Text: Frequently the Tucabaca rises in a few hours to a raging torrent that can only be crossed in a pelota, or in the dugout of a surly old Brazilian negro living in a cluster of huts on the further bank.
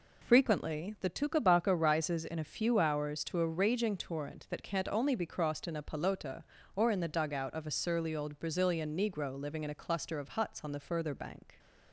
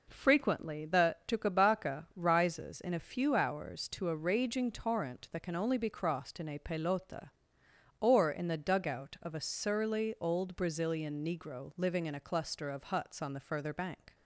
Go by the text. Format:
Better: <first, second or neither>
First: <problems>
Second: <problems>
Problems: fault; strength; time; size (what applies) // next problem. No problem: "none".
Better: second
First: says "can't" for "can"; at 4.6 s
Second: none